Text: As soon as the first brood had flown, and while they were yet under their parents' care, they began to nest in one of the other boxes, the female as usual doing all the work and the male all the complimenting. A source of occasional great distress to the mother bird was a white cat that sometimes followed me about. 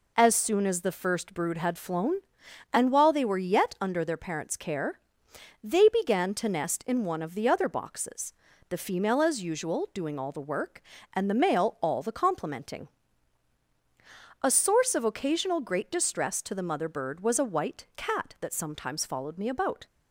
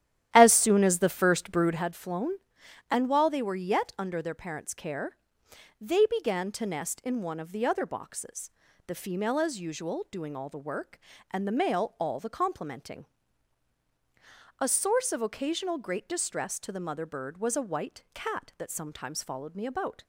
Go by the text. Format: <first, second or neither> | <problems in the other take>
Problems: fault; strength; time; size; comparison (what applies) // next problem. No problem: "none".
first | starts louder than the rest; strong; until 1.8 s; 12 dB